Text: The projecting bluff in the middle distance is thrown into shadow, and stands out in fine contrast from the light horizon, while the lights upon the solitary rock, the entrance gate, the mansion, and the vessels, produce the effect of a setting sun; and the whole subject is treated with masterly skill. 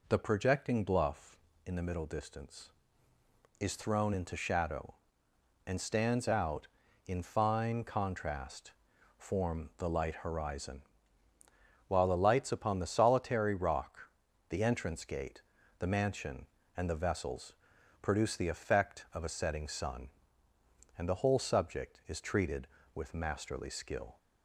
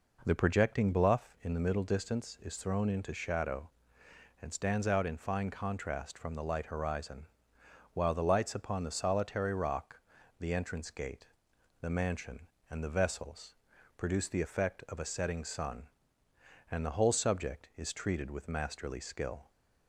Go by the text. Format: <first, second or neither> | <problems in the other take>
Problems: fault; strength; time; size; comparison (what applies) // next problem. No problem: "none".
second | says "form" for "from"; at 9.1 s